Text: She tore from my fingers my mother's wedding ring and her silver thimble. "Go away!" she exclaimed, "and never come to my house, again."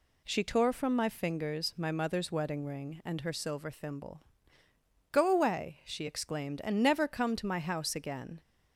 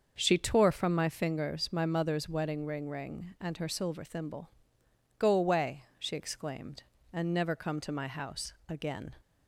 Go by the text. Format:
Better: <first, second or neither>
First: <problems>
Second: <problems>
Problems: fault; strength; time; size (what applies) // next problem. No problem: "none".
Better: first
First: none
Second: starts louder than the rest; until 1.2 s; 6.5 dB // says "ring" twice; at 2.8 s